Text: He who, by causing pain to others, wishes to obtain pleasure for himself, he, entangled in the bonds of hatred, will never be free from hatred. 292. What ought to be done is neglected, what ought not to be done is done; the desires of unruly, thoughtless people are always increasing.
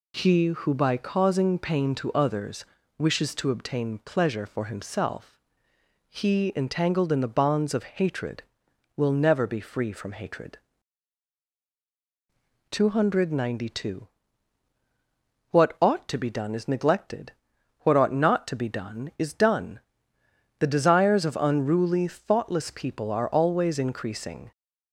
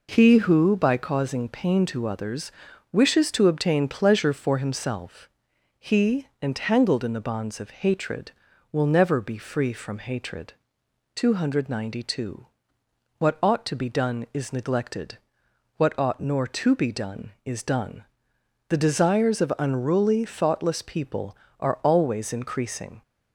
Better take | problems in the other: first | says "nor" for "not"; at 16.1 s

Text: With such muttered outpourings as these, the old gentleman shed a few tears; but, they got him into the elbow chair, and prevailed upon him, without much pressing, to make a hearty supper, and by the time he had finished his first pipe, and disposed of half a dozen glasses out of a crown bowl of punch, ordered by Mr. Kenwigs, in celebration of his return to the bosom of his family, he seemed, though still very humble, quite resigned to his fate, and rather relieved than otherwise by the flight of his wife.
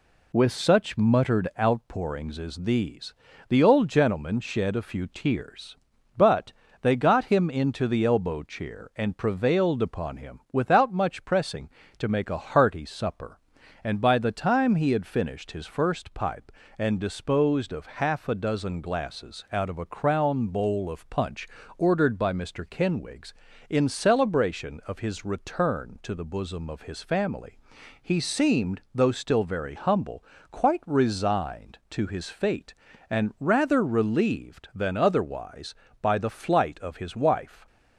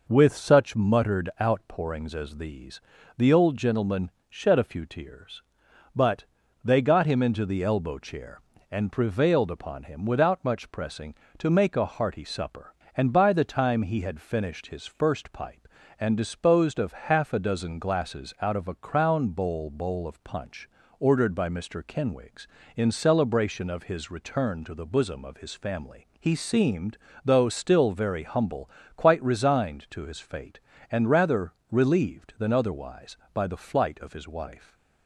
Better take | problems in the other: first | pauses between "gentleman" and "shed"; slight; at 4.0 s; 0.20 s long // says "bowl" twice; at 19.6 s // pauses between "rather" and "relieved"; slight; at 31.5 s; 0.18 s long

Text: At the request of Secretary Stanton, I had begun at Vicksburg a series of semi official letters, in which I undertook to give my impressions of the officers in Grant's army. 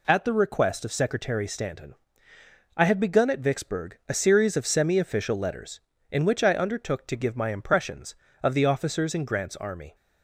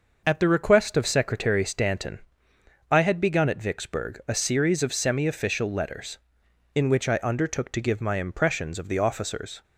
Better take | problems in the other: first | stops before "in Grant's army"; at 9.6 s

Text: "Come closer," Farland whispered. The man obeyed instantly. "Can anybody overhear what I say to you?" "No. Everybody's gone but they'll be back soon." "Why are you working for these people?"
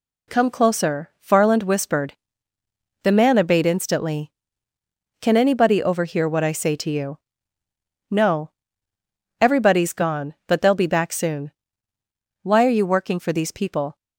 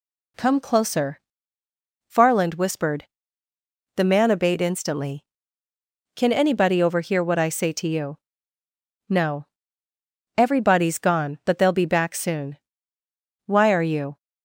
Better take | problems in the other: first | stops before "working for these people"; at 14.1 s

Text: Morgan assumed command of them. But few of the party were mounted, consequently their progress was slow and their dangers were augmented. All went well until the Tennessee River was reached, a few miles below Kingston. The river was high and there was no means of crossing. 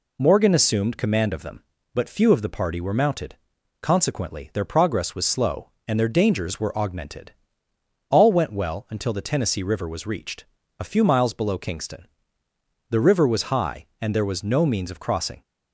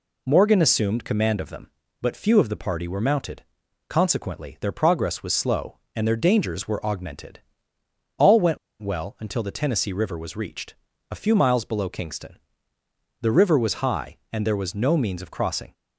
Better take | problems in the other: first | pauses between "went" and "well"; slight; at 8.5 s; 0.24 s long

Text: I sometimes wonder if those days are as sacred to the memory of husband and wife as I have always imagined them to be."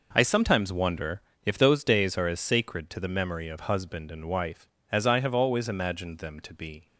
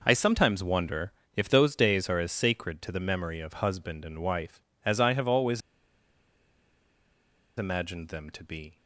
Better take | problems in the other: first | pauses between "wonder" and "if"; slight; at 1.1 s; 0.24 s long; slight in the first // pauses between "always" and "imagined"; strong; at 5.6 s; 1.9 s long

